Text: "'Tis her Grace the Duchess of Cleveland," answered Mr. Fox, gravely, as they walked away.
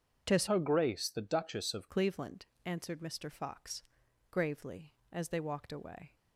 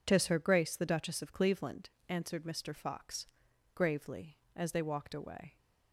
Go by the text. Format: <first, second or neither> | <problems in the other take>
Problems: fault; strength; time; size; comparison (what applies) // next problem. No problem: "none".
second | starts louder than the rest; strong; until 1.2 s; 8 dB // changes voice from "her" to "of"; from 0.4 to 1.8 s; 1.4 s long